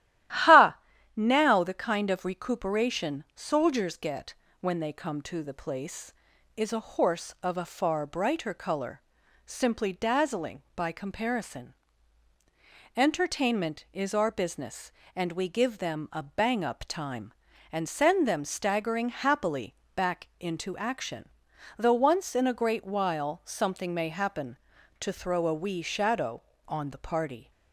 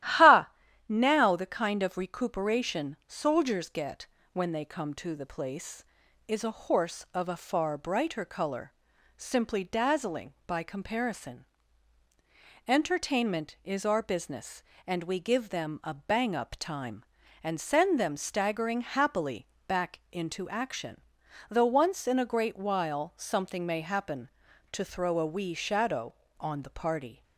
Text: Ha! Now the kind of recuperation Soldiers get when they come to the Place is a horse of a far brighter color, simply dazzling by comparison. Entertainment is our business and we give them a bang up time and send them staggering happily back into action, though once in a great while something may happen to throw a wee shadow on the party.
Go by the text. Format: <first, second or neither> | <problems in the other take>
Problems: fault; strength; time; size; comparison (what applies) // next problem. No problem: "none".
neither | starts louder than the rest; strong; the same in both // pauses between "get" and "when"; slight; the same in both // pauses between "happily" and "back"; slight; the same in both